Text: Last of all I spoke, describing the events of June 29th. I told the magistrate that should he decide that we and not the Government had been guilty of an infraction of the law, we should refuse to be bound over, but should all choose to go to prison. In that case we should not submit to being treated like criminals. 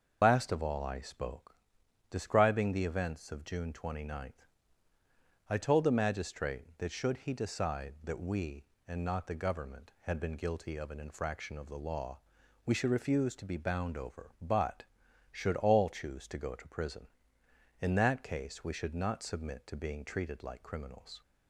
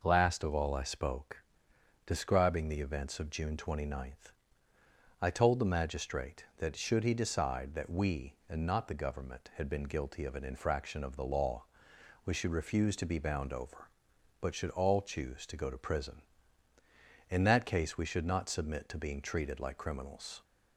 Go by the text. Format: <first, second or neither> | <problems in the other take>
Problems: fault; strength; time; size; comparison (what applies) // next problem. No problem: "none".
second | loses the start of "Last"; at 0.2 s; 115 ms // starts louder than the rest; until 1.2 s; 6.5 dB